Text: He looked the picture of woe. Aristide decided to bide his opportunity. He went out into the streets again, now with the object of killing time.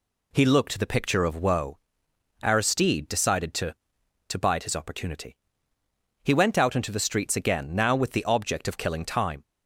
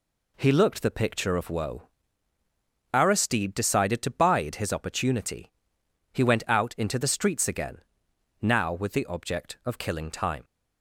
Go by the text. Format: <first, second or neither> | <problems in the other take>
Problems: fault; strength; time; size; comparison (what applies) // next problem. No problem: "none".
second | says "to" twice; at 4.2 s